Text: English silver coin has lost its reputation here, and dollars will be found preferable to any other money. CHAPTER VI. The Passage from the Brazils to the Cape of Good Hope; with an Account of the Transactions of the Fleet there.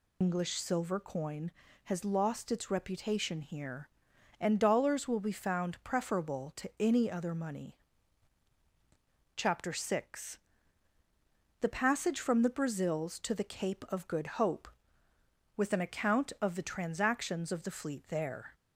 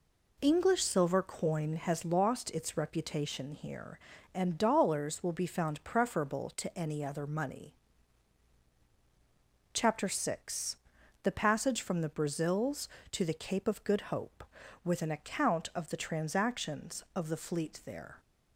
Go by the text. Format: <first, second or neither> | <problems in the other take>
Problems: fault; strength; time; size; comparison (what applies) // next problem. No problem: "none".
second | loses the start of "English"; at 0.2 s; 105 ms